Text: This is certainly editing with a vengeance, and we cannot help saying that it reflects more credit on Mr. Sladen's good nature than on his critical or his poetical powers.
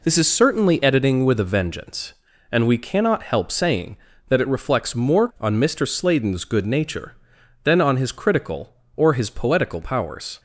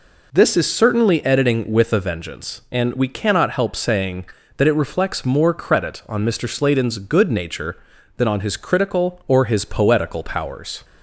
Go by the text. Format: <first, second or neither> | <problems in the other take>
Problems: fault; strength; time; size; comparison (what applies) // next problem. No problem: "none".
second | skips "credit"; at 5.3 s